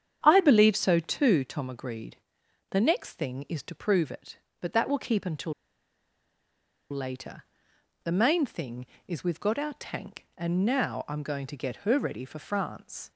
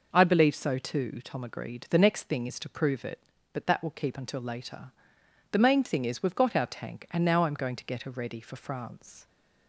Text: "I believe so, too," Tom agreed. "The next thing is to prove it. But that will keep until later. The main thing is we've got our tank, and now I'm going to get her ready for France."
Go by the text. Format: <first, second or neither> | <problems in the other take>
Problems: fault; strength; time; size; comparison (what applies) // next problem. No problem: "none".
second | starts louder than the rest; strong; until 1.2 s; 8.5 dB // pauses between "until" and "later"; strong; at 5.5 s; 1.3 s long